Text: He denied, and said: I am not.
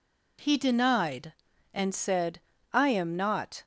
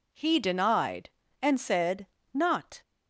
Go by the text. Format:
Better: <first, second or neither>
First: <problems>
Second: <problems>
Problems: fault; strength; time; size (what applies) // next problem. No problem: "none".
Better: first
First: none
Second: skips "I am"; at 2.1 s